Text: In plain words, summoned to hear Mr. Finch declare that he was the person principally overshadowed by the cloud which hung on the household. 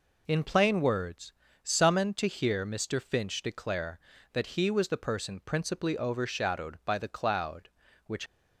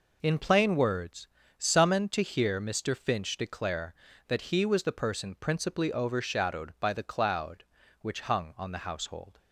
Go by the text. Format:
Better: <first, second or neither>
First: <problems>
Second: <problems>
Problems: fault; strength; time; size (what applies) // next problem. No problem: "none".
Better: second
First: stops before "hung on the household"; at 8.2 s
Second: none